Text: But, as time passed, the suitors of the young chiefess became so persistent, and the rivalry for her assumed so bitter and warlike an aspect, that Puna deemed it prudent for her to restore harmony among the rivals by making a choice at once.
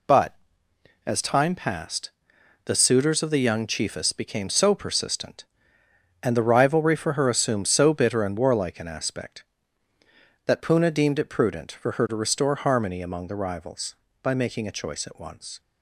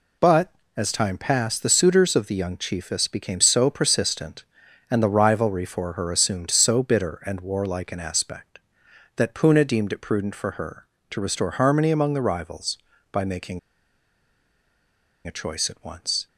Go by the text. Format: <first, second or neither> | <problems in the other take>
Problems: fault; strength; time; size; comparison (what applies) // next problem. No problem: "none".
first | pauses between "making" and "a"; strong; at 13.5 s; 1.6 s long